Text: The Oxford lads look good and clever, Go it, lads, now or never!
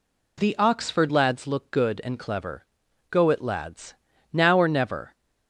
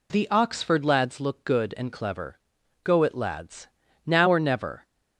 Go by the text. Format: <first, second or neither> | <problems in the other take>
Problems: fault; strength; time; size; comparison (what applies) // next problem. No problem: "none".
neither | none